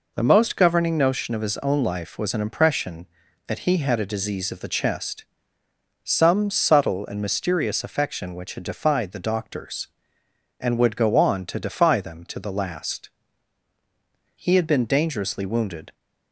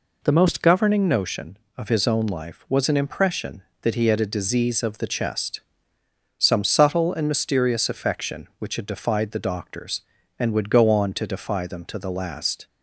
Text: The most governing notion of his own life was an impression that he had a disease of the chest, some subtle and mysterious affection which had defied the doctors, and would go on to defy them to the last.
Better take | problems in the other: second | goes on to say "He had been dangerously wounded"; from 14.3 s on; 1.5 s long

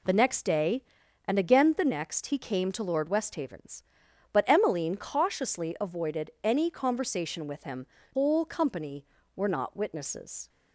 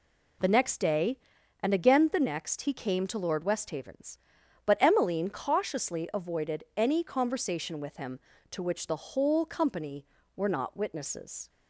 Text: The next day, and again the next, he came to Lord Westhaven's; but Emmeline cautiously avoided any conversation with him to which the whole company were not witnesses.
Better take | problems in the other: second | skips "to which the"; at 8.0 s

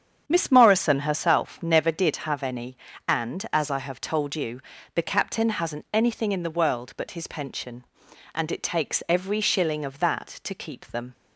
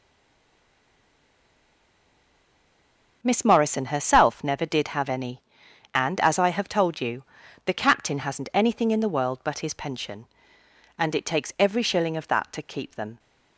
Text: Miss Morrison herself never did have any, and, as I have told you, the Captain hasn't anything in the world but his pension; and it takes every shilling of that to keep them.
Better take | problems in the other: first | stays silent before the first word; strong; until 3.2 s; 3.2 s long // starts louder than the rest; until 4.2 s; 6.5 dB; strong in the first

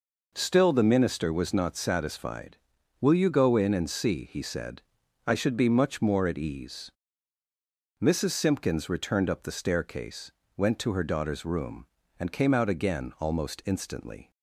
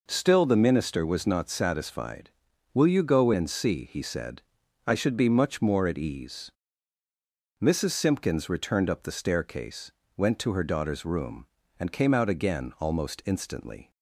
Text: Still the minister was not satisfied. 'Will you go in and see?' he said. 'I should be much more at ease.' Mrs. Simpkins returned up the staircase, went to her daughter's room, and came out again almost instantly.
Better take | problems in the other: first | skips "in"; at 3.3 s

